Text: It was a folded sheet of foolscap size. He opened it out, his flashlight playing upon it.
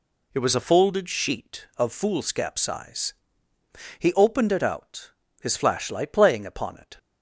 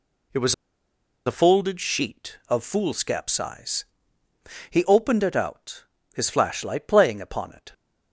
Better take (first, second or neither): first